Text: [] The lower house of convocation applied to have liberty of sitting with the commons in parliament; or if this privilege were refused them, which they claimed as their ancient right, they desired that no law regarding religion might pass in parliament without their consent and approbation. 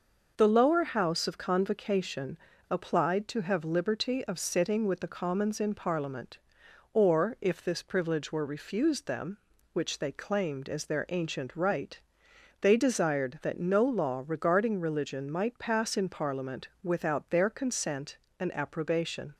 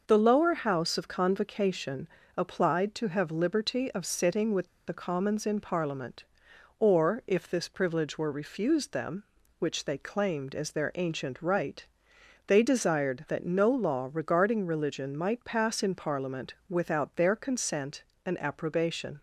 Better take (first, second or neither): first